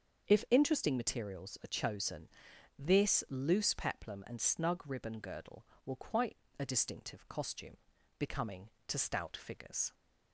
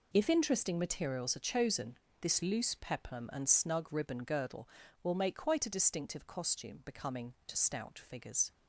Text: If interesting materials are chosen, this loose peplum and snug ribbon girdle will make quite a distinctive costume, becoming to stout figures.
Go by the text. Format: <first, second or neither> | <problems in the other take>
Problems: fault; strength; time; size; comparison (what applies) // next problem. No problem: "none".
second | starts louder than the rest; until 1.3 s; 7 dB // skips "make"; at 5.9 s // pauses between "quite" and "a"; slight; at 6.3 s; 0.22 s long